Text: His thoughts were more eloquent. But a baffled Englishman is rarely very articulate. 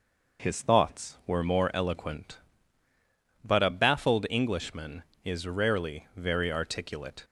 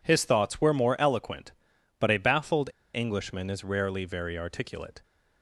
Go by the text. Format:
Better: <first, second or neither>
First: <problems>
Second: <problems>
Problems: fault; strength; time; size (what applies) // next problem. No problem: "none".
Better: first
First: none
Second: pauses between "baffled" and "Englishman"; slight; at 2.6 s; 0.26 s long